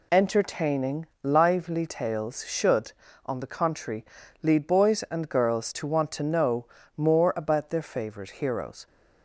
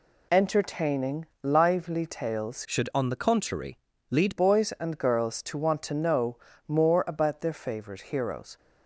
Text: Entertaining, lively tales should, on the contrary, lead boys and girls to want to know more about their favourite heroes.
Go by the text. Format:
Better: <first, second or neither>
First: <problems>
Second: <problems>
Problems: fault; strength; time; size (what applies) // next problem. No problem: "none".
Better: first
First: pauses between "know" and "more"; slight; at 6.6 s; 0.32 s long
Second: changes voice from "should" to "lead"; from 2.6 to 4.3 s; 1.7 s long // pauses between "know" and "more"; slight; at 6.3 s; 0.32 s long